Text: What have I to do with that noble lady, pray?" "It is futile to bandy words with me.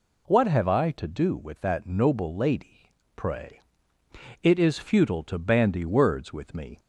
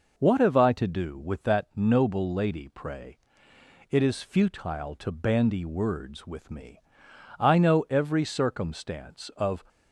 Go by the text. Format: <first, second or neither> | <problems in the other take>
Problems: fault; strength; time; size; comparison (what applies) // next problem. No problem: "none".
first | goes on to say "I know every circumstance of"; strong; from 7.3 s on; 2.2 s long